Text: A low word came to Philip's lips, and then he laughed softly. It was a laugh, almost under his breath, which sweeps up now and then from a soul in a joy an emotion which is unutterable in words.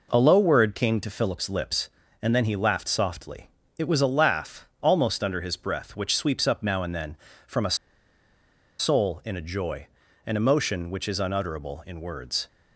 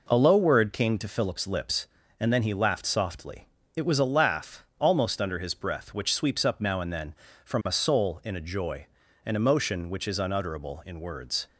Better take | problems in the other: second | pauses between "a" and "soul"; at 7.7 s; 1.0 s long // pauses between "joy" and "an"; slight; at 9.8 s; 0.36 s long; slight in the second

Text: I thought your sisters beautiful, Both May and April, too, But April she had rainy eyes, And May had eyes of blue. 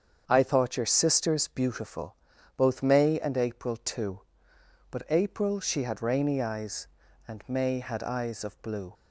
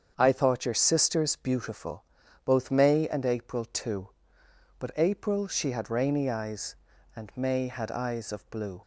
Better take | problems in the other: neither | starts louder than the rest; strong; the same in both

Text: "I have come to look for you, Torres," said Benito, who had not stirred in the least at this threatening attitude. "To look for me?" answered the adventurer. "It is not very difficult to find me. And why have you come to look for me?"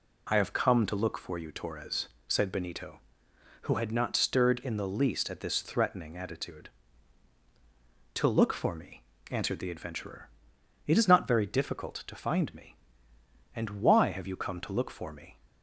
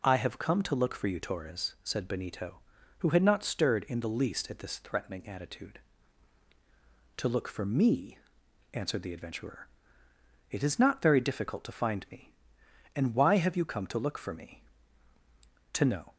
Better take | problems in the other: first | goes on to say "To know"; slight; from 15.7 s on; 0.40 s long

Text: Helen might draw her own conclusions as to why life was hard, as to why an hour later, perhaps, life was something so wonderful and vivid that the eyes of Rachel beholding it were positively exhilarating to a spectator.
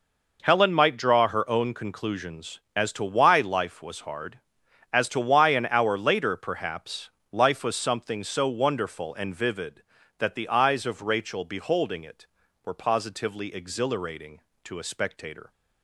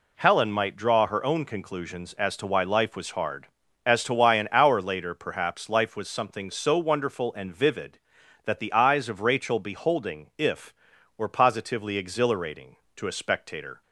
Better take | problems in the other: first | says "if" for "it"; at 10.3 s

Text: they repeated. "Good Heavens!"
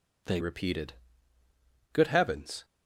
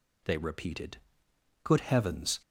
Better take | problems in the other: second | changes voice at "repeated"; from 0.4 s on; 2.2 s long

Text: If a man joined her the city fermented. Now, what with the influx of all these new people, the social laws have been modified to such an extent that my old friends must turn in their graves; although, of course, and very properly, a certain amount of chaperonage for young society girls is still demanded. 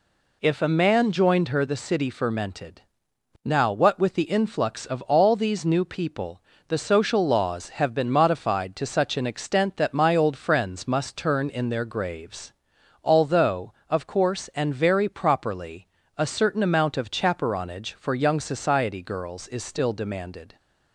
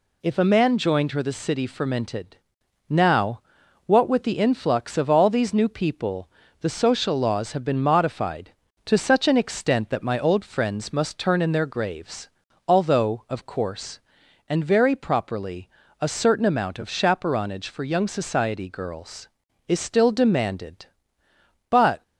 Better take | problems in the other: first | goes on to say "But"; slight; from 21.6 s on; 0.32 s long

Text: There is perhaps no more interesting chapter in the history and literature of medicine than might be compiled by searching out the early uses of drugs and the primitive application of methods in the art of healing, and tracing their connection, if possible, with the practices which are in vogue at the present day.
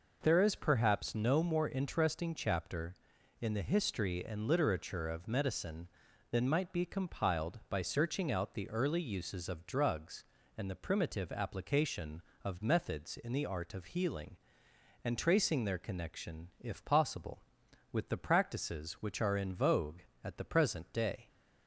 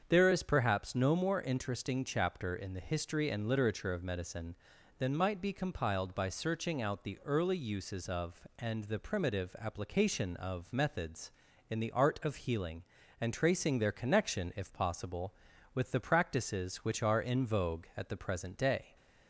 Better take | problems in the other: first | starts louder than the rest; until 1.1 s; 7 dB // skips "drugs"; at 8.4 s

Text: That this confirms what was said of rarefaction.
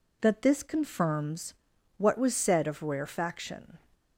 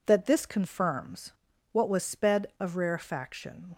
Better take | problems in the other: first | pauses between "confirms" and "what"; at 1.3 s; 0.40 s long; also in the first // says "sped" for "said"; at 2.0 s

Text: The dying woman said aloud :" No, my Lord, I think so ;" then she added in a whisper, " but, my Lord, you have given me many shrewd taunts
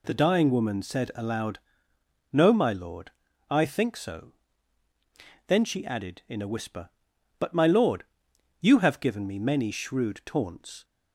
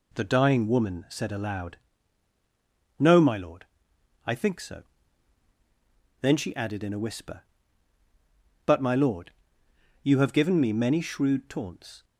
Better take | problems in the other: neither | none

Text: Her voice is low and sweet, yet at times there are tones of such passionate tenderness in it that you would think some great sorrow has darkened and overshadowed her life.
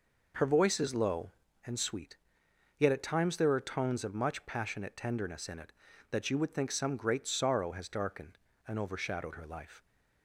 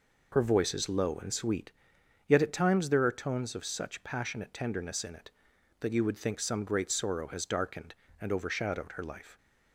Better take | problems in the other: second | says "much" for "such"; at 4.1 s

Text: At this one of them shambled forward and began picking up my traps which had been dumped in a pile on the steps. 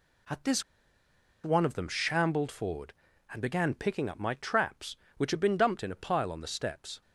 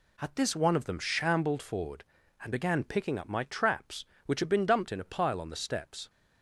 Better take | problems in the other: second | pauses between "this" and "one"; noticeable; at 0.6 s; 0.81 s long

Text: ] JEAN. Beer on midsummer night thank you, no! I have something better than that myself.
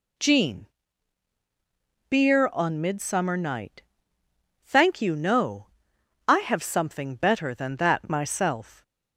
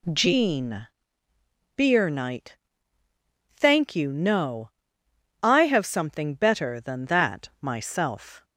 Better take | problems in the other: first | skips "on midsummer"; at 2.1 s // pauses between "night" and "thank"; at 2.5 s; 1.0 s long; noticeable in the first

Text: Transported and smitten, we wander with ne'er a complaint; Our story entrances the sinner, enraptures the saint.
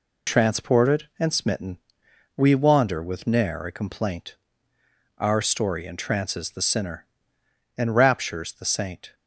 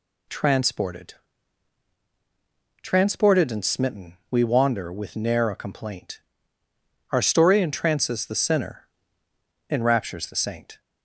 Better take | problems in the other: first | says "Transported" twice; at 2.8 s

